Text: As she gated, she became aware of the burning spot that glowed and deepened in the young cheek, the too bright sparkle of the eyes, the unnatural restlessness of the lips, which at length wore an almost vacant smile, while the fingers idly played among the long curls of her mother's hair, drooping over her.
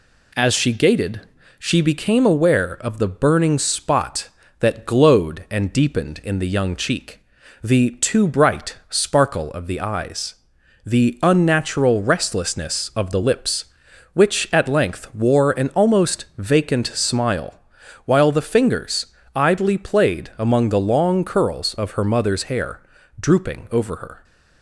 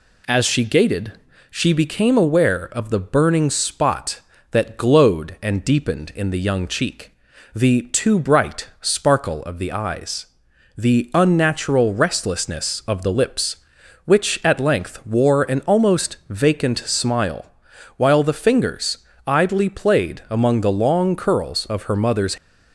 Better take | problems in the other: first | pauses between "fingers" and "idly"; slight; at 18.9 s; 0.28 s long; slight in the first // stops before "hair drooping over her"; at 22.3 s

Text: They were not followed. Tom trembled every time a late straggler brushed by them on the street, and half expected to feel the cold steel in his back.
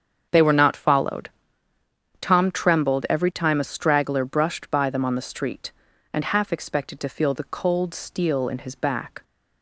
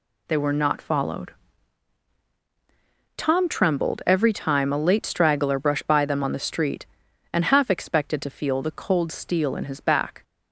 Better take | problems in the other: second | starts louder than the rest; strong; until 1.3 s; 7.5 dB // skips "late"; at 3.6 s

